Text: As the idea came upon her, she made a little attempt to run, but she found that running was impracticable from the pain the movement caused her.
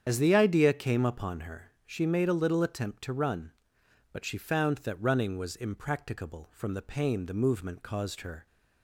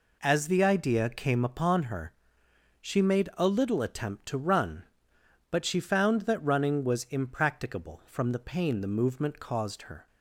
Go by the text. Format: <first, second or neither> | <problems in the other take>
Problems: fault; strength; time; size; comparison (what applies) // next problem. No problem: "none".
second | loses the start of "As"; at 0.0 s; 50 ms // starts louder than the rest; strong; until 1.0 s; 8.5 dB